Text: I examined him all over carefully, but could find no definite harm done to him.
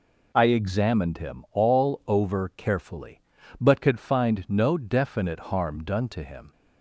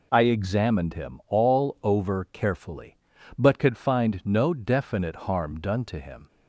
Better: neither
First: none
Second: none

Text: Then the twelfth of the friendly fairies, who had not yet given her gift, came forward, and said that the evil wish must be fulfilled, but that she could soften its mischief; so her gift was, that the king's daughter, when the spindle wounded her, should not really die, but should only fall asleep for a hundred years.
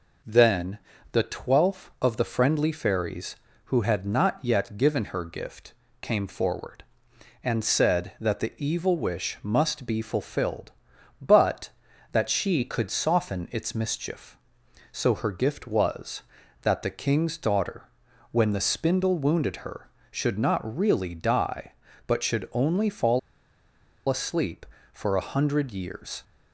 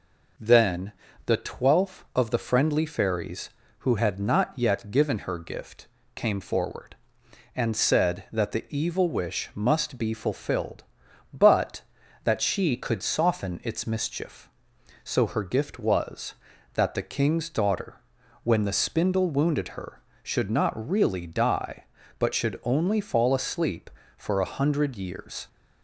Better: second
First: pauses between "Then" and "the"; slight; at 0.7 s; 0.34 s long // pauses between "fall" and "asleep"; noticeable; at 23.1 s; 0.89 s long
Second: pauses between "Then" and "the"; slight; at 0.9 s; 0.34 s long

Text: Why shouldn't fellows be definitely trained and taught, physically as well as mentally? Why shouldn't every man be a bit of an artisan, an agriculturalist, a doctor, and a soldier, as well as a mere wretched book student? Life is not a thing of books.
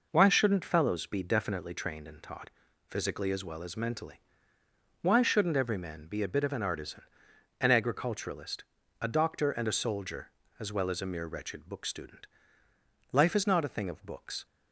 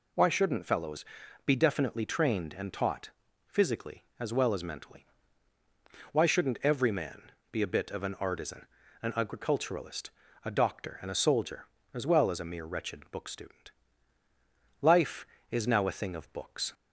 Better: first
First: none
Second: pauses between "fellows" and "be"; at 1.0 s; 0.42 s long // pauses between "man" and "be"; slight; at 7.3 s; 0.20 s long // says "now" for "not"; at 15.6 s

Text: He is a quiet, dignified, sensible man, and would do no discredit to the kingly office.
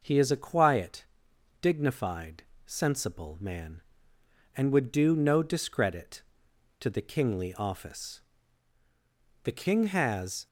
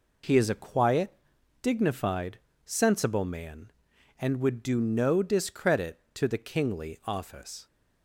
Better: second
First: goes on to say "The King has"; noticeable; from 9.4 s on; 1.0 s long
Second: none

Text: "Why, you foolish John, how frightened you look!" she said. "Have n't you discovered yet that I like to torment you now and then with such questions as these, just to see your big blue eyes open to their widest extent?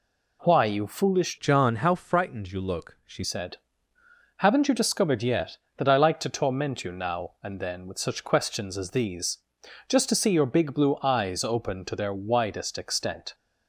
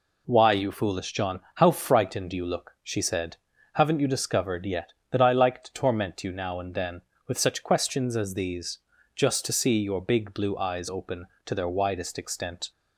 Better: second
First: changes voice from "John" to "she"; from 1.3 to 3.2 s; 1.9 s long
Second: none

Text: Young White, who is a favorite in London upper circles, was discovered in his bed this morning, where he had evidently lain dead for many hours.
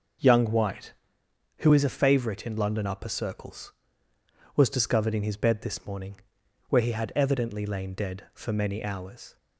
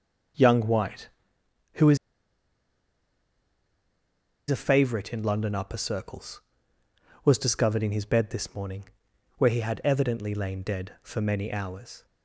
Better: first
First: none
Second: starts louder than the rest; noticeable; until 4.5 s; 6 dB // pauses between "is" and "a"; strong; at 1.9 s; 2.5 s long

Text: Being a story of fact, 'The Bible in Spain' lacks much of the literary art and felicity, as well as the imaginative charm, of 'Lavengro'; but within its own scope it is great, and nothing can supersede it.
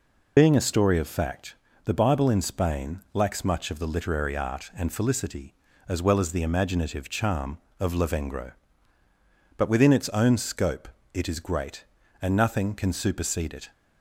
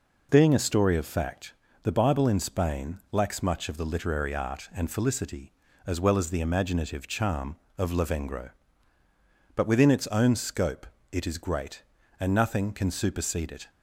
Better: second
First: loses the start of "Being"; at 0.3 s; 50 ms // pauses between "scope" and "it"; slight; at 10.8 s; 0.24 s long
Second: pauses between "scope" and "it"; slight; at 10.8 s; 0.24 s long

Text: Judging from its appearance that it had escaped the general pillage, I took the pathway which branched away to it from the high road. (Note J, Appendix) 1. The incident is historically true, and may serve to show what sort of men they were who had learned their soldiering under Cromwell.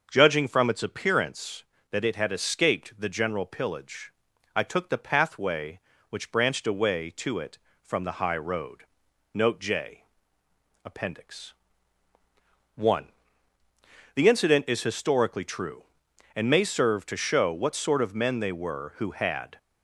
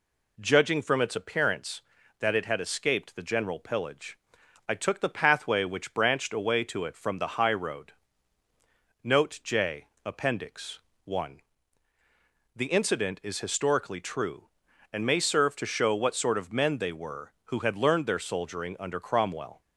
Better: second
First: starts louder than the rest; until 1.1 s; 6.5 dB // stops before "learned their soldiering under Cromwell"; at 19.5 s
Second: none

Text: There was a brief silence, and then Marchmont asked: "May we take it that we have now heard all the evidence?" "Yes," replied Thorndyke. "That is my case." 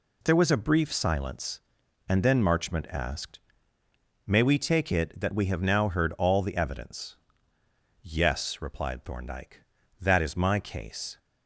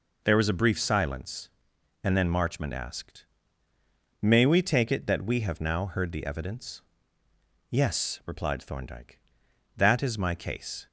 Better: first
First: none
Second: skips "all"; at 6.1 s

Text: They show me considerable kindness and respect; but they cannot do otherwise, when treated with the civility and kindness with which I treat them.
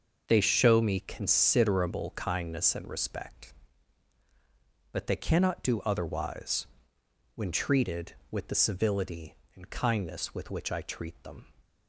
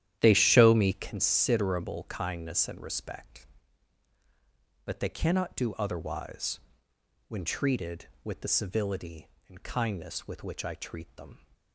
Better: first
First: none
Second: starts louder than the rest; strong; until 1.1 s; 11 dB

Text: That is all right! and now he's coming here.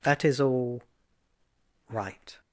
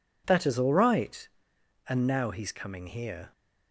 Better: second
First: pauses between "all" and "right"; at 0.8 s; 1.0 s long // stops before "and now he's coming here"; at 2.4 s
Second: none

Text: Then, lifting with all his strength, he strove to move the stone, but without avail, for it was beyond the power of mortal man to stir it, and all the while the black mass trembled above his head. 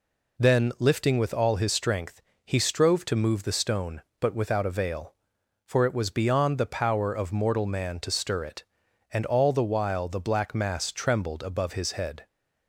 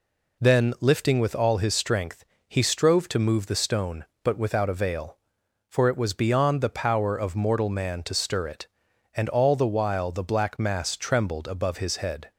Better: neither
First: none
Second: none

